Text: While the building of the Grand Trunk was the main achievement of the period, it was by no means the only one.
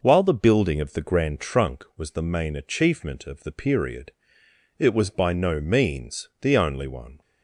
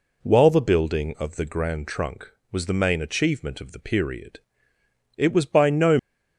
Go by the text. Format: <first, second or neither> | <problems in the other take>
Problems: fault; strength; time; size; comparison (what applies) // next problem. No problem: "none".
first | stops before "means the only one"; at 5.9 s